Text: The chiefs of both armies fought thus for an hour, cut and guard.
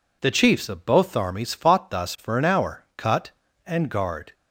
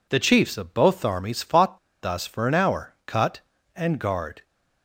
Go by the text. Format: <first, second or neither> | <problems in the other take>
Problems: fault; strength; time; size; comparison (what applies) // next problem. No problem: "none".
first | pauses between "fought" and "thus"; slight; at 1.7 s; 0.24 s long